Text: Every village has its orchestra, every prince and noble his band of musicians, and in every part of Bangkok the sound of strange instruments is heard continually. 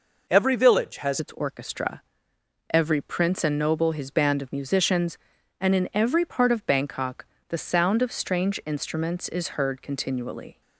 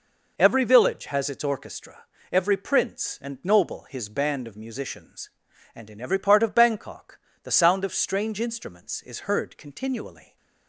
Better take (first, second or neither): second